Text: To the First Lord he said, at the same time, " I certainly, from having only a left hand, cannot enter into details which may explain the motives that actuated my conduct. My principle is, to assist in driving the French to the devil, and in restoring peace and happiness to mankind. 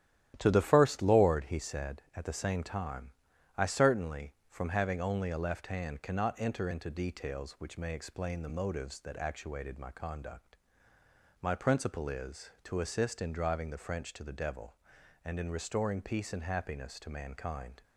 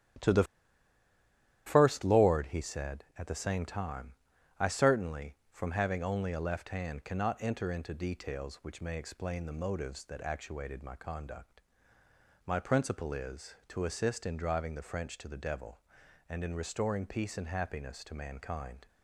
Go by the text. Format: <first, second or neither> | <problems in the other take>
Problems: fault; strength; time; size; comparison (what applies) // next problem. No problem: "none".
first | starts louder than the rest; strong; until 2.4 s; 9.5 dB; strong in the first // pauses between "the" and "First"; at 0.4 s; 1.2 s long